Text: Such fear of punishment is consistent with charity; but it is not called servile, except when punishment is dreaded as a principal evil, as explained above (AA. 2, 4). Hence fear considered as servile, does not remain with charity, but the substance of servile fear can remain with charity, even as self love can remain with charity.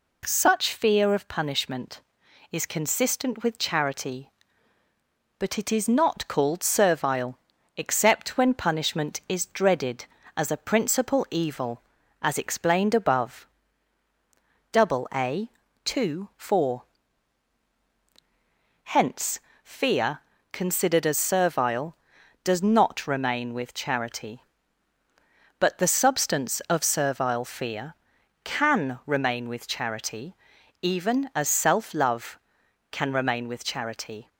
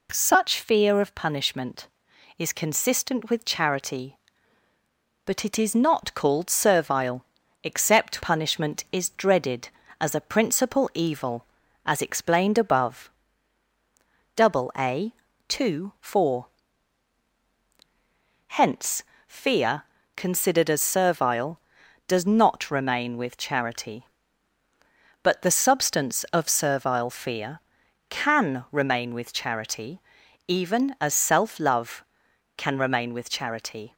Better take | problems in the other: first | skips "when"; at 8.2 s // pauses between "Hence" and "fear"; slight; at 19.0 s; 0.22 s long; slight in the first // pauses between "fear" and "considered"; slight; at 19.8 s; 0.32 s long; slight in the first

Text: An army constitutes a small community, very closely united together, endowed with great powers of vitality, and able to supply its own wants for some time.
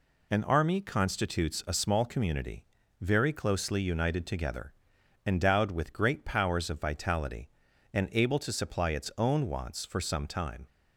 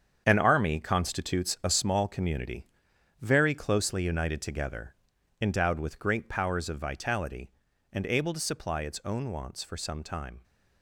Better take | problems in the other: first | gets quieter; strong; throughout; 10 dB

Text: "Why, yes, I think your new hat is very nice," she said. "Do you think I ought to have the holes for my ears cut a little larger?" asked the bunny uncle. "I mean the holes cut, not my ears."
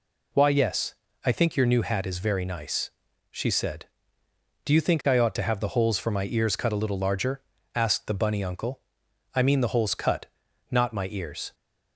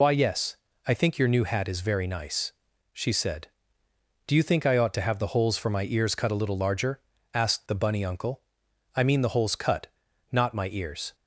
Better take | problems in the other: first | loses the start of "Why"; at 0.0 s; 55 ms

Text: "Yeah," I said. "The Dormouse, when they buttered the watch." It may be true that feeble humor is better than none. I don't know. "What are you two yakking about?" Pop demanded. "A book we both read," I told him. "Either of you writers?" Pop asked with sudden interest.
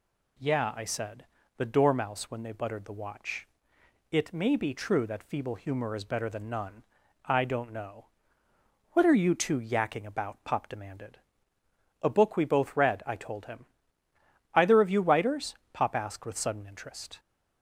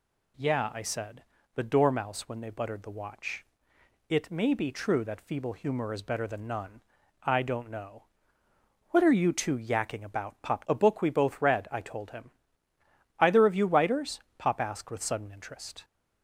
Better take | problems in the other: first | skips "demanded"; at 10.6 s

